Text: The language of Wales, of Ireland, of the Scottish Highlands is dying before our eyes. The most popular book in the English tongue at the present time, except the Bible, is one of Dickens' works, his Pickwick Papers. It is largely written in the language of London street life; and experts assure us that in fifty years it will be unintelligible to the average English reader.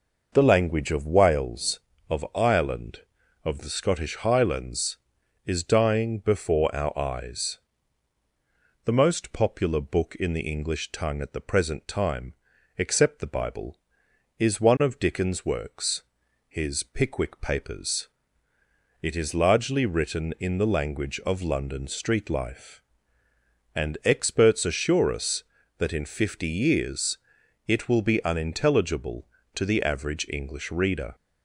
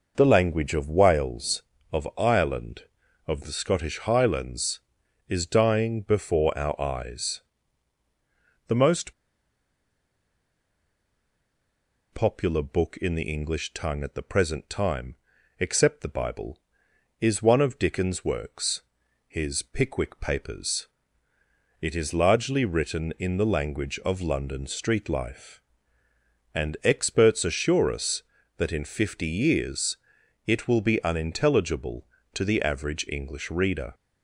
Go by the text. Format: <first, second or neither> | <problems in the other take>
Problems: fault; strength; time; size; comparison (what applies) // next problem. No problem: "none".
first | pauses between "most" and "popular"; strong; at 9.1 s; 3.0 s long // pauses between "years" and "it"; noticeable; at 29.9 s; 0.50 s long; noticeable in the first